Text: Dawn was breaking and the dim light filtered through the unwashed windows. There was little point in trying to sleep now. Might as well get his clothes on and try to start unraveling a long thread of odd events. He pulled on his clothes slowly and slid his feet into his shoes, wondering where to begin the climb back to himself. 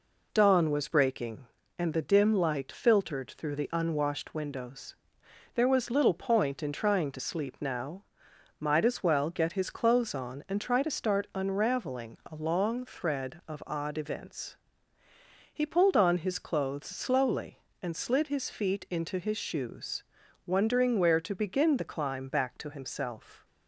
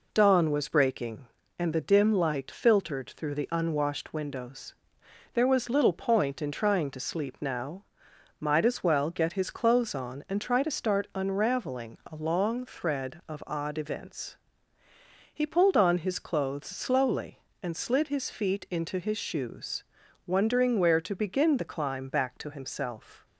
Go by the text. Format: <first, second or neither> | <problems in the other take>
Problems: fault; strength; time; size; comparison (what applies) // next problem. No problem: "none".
neither | none